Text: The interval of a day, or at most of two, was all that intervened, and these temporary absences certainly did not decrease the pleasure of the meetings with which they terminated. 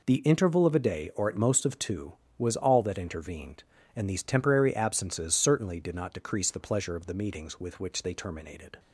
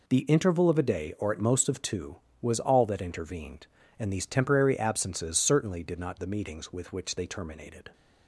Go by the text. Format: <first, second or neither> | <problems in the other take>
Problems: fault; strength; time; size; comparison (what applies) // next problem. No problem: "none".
first | skips "decrease the pleasure of"; at 6.1 s